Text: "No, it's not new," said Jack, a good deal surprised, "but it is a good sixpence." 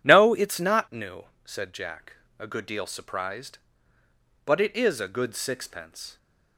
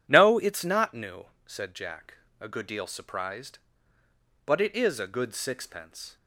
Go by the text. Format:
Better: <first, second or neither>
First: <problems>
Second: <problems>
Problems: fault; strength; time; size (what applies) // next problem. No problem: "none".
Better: neither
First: none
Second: none